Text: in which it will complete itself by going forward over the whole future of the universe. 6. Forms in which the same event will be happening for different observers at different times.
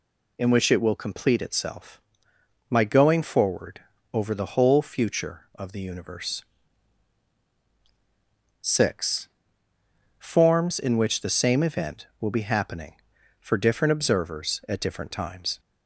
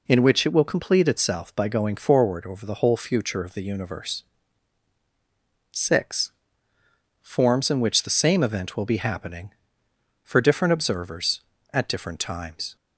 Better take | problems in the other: second | says "my" for "by"; at 2.6 s // pauses between "forward" and "over"; slight; at 3.8 s; 0.32 s long

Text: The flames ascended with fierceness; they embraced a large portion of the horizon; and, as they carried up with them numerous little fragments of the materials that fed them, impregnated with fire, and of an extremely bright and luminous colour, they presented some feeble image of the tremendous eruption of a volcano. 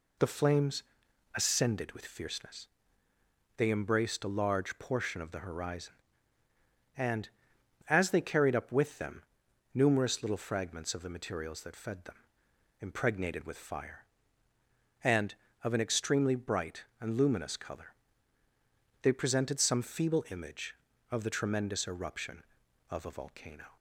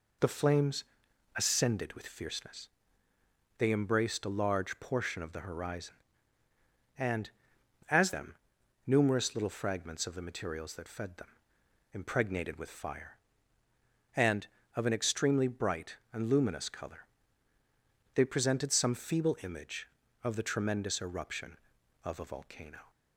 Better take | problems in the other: first | pauses between "flames" and "ascended"; noticeable; at 0.8 s; 0.54 s long; noticeable in the first // skips "they carried up with"; at 8.1 s // pauses between "them" and "numerous"; noticeable; at 8.3 s; 0.54 s long; noticeable in the first

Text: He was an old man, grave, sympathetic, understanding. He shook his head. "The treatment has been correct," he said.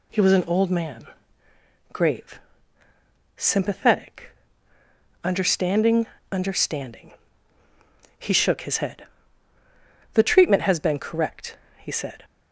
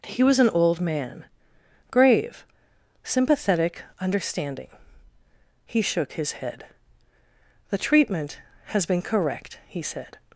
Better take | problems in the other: second | says "understanding" twice; at 6.3 s

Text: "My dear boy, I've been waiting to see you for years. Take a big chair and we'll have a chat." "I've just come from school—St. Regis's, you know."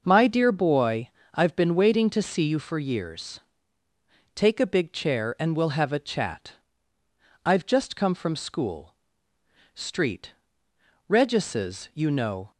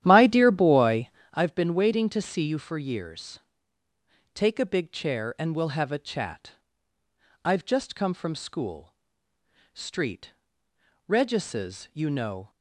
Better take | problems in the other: first | starts louder than the rest; strong; until 1.4 s; 11.5 dB

